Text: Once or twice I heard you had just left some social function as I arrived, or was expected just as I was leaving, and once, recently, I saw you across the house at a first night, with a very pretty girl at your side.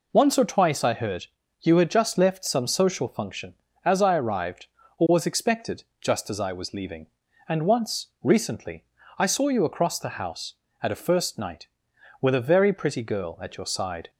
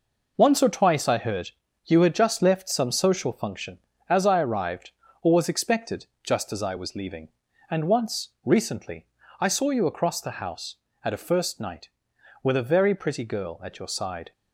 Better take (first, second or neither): first